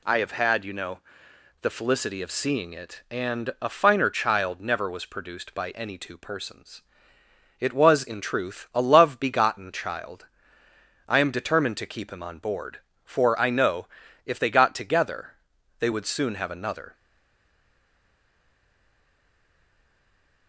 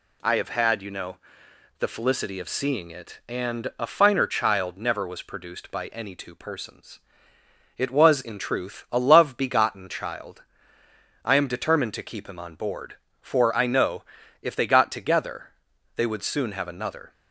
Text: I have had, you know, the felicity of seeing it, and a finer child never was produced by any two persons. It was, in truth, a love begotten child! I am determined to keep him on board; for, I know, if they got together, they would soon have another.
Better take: second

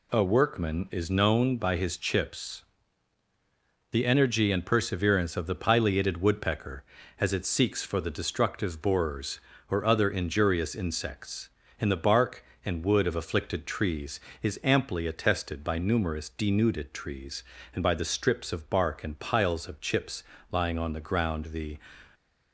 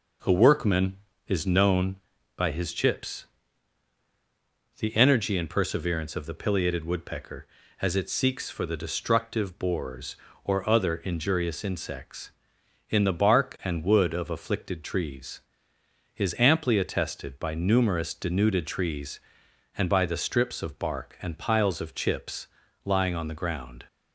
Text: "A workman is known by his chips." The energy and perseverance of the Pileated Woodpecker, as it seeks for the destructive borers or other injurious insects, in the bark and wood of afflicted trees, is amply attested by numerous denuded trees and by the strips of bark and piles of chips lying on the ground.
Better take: second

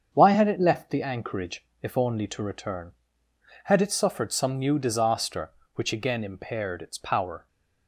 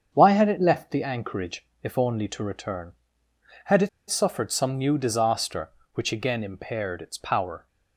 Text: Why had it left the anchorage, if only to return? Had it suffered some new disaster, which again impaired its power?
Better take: first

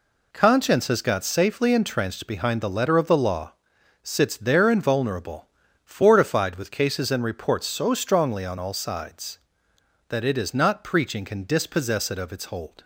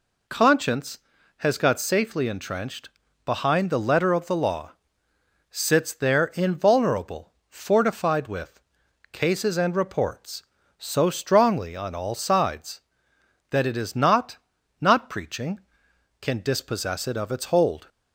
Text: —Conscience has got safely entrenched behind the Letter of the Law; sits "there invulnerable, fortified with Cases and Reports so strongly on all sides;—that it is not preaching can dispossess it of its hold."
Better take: first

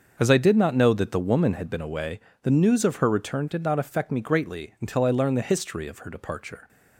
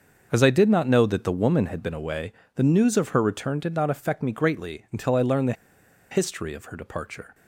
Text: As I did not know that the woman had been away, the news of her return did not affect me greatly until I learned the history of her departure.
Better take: first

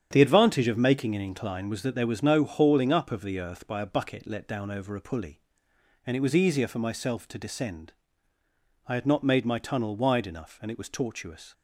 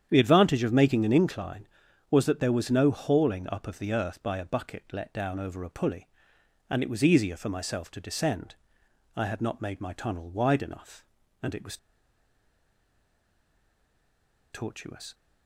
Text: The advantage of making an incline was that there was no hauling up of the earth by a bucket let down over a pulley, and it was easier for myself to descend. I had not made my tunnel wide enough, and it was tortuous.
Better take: first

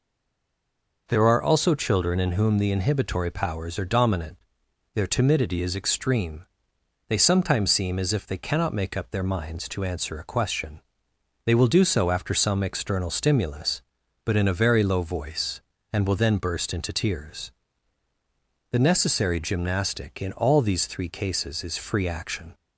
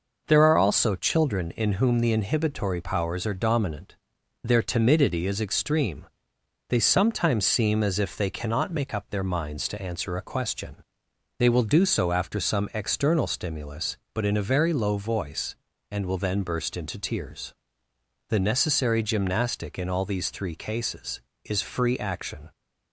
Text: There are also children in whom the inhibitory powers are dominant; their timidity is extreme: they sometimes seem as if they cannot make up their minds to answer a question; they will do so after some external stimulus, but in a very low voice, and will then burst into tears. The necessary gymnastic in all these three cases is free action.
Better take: second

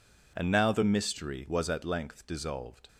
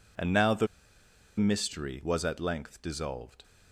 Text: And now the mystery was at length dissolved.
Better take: first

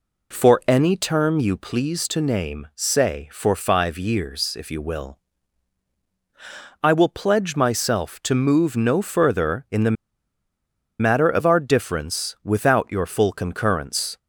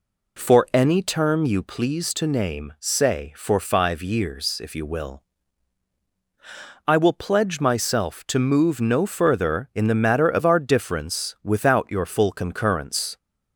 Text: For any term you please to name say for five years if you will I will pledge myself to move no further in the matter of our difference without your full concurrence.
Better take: second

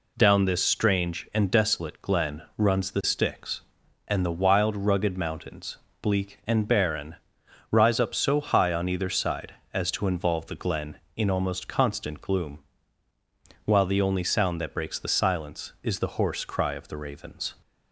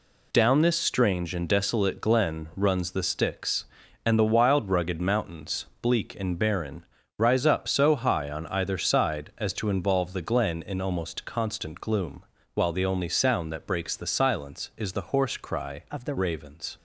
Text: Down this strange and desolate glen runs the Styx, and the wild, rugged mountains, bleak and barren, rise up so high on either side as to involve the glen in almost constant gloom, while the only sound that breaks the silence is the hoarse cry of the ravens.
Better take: first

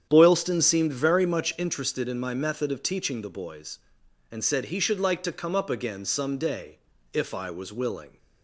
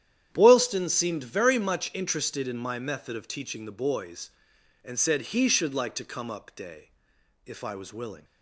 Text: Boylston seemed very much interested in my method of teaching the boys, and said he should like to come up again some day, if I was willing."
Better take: first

